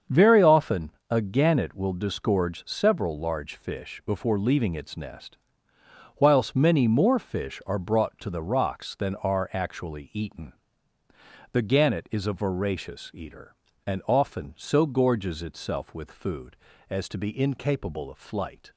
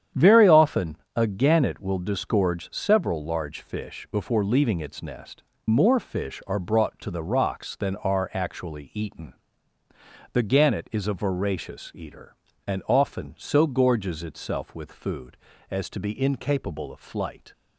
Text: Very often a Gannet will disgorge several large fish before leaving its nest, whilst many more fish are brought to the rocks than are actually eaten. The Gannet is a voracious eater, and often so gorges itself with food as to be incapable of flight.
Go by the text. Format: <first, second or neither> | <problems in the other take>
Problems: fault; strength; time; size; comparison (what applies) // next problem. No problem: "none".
first | starts louder than the rest; strong; until 1.3 s; 9 dB; strong in the first // pauses between "often" and "a"; slight; at 0.9 s; 0.18 s long; slight in the first // skips "whilst many"; at 5.5 s